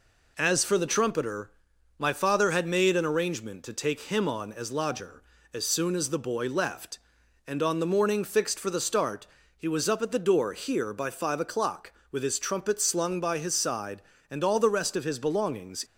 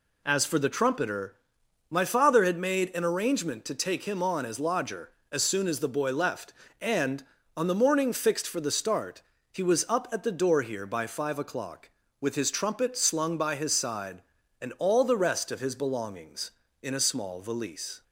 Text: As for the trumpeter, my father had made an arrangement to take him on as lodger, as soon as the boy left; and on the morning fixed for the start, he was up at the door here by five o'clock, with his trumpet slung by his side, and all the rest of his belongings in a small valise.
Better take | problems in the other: second | stops before "in a small valise"; at 15.8 s

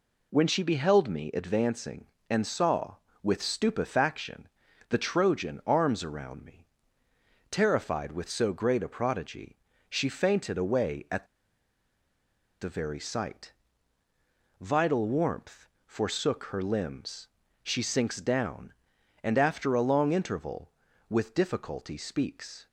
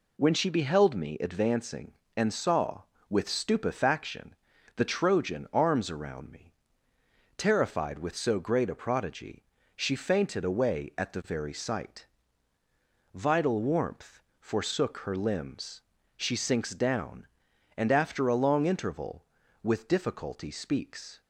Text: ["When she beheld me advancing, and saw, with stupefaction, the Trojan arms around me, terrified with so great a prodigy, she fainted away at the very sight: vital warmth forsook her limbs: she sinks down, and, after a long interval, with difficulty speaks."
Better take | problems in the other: second | pauses between "at" and "the"; strong; at 11.2 s; 1.3 s long // pauses between "warmth" and "forsook"; slight; at 15.6 s; 0.20 s long; slight in the second

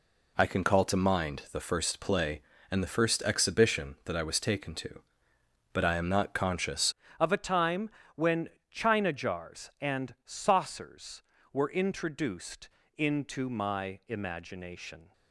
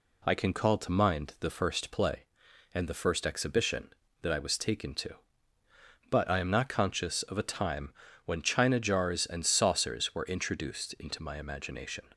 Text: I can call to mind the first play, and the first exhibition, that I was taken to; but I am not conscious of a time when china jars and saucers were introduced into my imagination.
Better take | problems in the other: second | changes voice at "of"; from 7.2 s on; 7.9 s long // pauses between "time" and "when"; slight; at 7.8 s; 0.28 s long; slight in the second // pauses between "when" and "china"; slight; at 8.4 s; 0.24 s long // pauses between "introduced" and "into"; slight; at 12.6 s; 0.28 s long

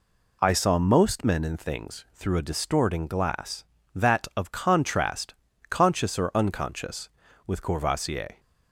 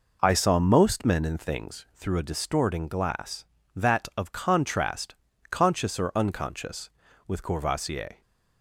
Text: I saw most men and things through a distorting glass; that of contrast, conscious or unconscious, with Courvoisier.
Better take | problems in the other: first | starts louder than the rest; noticeable; until 1.8 s; 4.5 dB

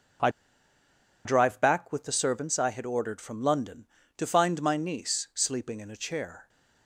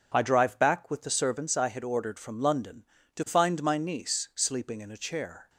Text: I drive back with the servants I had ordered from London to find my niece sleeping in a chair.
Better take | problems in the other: second | pauses between "I" and "drive"; noticeable; at 0.2 s; 0.96 s long

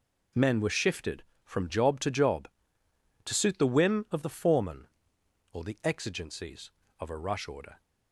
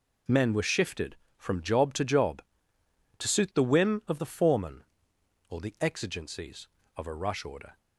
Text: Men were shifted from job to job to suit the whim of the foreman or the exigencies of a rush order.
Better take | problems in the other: neither | none

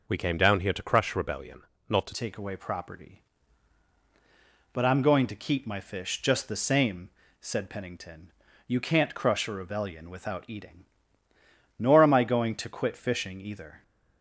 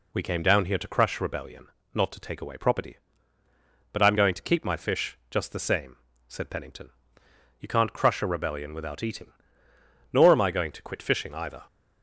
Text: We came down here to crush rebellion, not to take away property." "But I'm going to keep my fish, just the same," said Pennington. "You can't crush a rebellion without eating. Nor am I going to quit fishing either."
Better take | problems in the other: second | changes voice at "take"; from 2.1 s on; 11.7 s long

